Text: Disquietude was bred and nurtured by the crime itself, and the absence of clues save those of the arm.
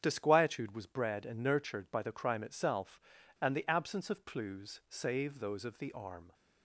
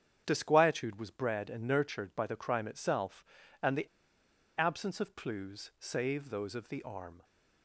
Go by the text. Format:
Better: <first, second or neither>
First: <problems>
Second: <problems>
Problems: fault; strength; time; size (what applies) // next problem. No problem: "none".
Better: first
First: starts louder than the rest; strong; until 1.0 s; 8.5 dB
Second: starts louder than the rest; strong; until 1.2 s; 8 dB // pauses between "the" and "absence"; noticeable; at 3.8 s; 0.71 s long